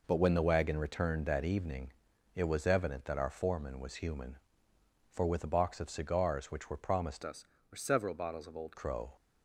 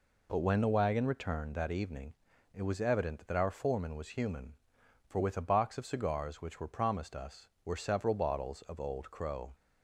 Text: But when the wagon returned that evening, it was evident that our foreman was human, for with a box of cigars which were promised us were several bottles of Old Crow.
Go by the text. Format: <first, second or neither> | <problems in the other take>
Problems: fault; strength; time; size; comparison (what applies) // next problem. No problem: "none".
second | changes voice from "us" to "Old"; from 7.2 to 8.7 s; 1.5 s long